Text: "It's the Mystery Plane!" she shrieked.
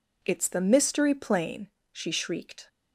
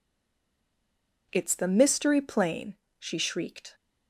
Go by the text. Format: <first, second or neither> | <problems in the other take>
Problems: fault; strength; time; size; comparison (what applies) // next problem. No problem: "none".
first | stays silent before the first word; noticeable; until 1.3 s; 1.3 s long